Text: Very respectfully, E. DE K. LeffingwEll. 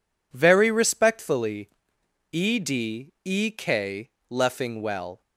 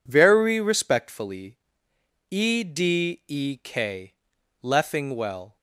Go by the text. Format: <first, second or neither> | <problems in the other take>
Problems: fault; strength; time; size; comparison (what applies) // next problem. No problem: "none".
neither | none